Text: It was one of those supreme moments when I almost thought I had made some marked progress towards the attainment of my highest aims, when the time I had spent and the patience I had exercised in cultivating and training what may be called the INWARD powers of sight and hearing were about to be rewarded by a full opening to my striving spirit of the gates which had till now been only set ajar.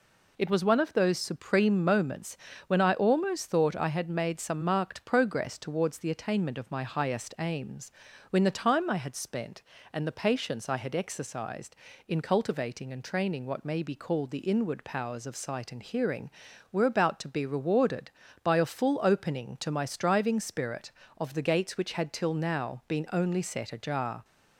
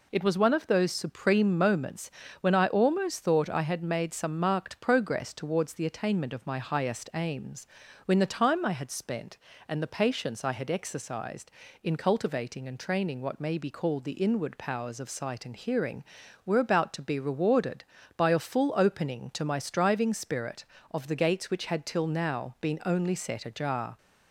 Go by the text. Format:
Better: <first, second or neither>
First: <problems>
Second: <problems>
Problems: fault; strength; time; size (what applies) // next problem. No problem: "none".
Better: neither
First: pauses between "moments" and "when"; slight; at 2.3 s; 0.32 s long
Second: pauses between "moments" and "when"; slight; at 2.0 s; 0.32 s long